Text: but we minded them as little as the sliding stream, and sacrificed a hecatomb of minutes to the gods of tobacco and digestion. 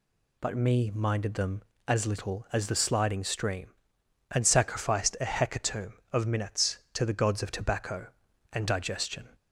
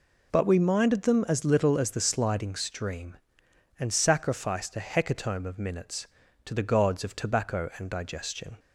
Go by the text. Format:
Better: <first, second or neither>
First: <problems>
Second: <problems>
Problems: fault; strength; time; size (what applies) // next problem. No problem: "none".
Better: second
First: says "me" for "we"; at 0.5 s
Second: none